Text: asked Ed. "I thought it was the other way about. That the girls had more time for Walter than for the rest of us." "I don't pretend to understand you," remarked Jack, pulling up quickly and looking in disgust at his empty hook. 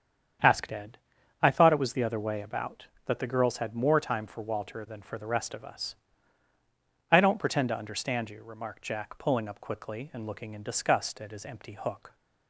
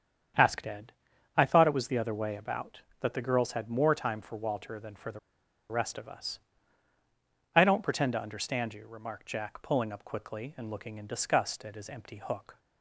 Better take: first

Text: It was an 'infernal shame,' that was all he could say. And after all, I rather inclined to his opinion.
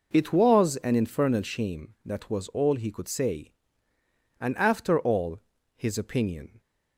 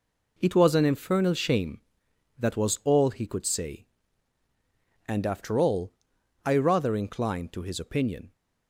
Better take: second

